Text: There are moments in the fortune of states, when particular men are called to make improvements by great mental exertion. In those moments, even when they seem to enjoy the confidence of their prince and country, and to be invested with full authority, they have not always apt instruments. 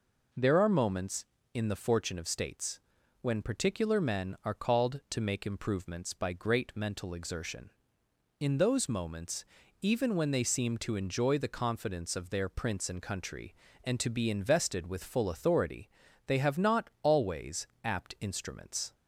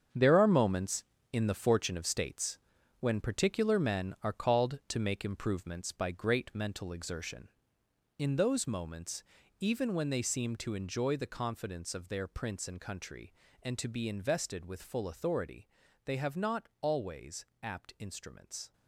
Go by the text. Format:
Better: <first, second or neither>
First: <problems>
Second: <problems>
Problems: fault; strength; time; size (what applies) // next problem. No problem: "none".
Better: first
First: pauses between "always" and "apt"; slight; at 17.6 s; 0.18 s long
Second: gets quieter; strong; throughout; 9.5 dB // pauses between "always" and "apt"; slight; at 17.4 s; 0.18 s long